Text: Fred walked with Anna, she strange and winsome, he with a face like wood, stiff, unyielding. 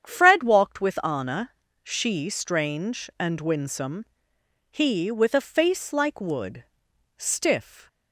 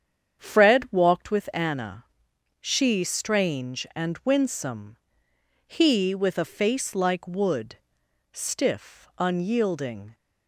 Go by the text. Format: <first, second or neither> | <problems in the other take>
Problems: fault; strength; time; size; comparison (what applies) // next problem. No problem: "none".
second | starts louder than the rest; strong; until 1.1 s; 8.5 dB; strong in the second // stops before "unyielding"; at 7.8 s